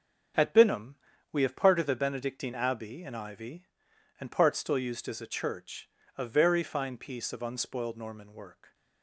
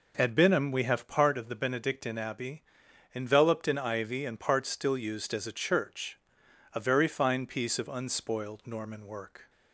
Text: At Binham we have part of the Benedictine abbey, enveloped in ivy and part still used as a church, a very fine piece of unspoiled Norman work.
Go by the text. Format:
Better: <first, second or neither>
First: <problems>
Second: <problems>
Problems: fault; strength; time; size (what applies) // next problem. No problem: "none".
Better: second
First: starts louder than the rest; strong; until 1.7 s; 7 dB // pauses between "Binham" and "we"; at 0.9 s; 0.38 s long // skips "enveloped"; at 3.0 s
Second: none